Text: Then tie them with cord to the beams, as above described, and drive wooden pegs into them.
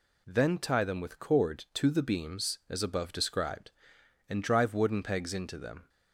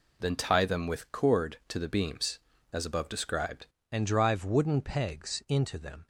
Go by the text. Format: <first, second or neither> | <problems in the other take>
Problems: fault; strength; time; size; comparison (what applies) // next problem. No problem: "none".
first | changes voice at "and"; from 3.9 s on; 2.1 s long